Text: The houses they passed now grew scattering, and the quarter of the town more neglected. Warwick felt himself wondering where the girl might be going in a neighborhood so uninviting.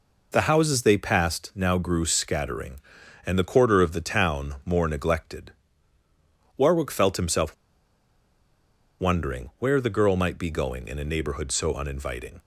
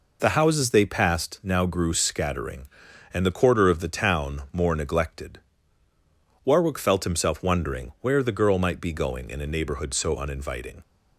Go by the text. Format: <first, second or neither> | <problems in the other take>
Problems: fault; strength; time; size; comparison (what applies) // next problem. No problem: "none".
second | pauses between "himself" and "wondering"; strong; at 7.5 s; 1.4 s long